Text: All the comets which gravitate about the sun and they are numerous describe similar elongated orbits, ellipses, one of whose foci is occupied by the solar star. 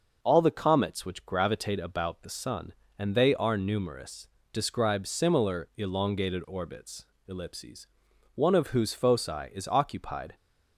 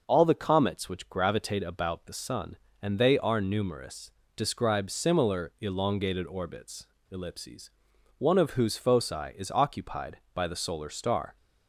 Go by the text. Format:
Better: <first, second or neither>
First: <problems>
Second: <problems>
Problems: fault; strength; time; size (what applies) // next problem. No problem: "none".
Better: second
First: pauses between "numerous" and "describe"; slight; at 4.2 s; 0.26 s long // stops before "by the solar star"; at 10.3 s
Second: pauses between "numerous" and "describe"; slight; at 4.1 s; 0.26 s long